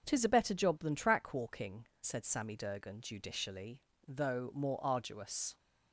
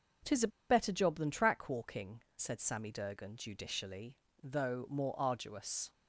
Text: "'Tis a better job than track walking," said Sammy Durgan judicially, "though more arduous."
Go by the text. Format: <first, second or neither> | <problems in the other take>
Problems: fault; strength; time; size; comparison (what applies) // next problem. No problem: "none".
first | starts louder than the rest; until 1.4 s; 7 dB; also in the first // pauses between "a" and "better"; slight; at 0.4 s; 0.22 s long